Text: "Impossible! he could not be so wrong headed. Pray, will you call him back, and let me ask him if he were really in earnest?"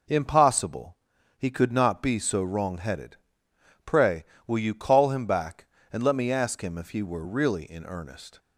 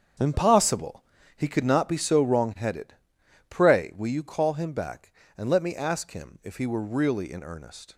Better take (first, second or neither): first